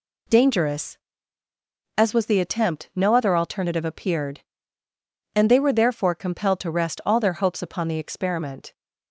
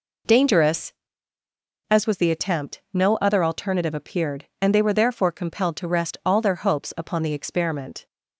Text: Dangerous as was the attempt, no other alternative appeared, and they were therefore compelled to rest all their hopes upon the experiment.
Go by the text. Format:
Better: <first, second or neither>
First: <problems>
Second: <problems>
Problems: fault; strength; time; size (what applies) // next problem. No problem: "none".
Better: first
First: none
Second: starts louder than the rest; until 1.5 s; 3.5 dB